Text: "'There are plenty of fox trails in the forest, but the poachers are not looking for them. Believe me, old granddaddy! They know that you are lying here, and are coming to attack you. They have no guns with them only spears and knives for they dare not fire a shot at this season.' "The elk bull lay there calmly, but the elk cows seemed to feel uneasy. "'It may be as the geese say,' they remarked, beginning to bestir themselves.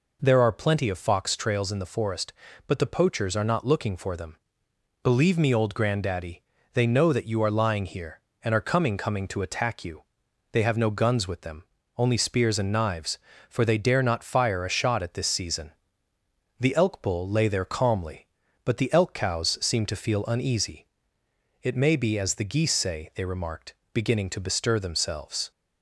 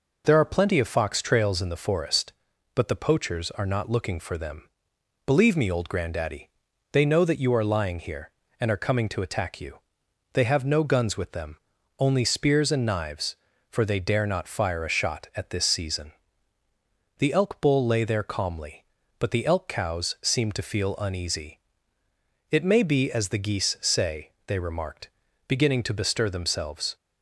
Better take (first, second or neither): second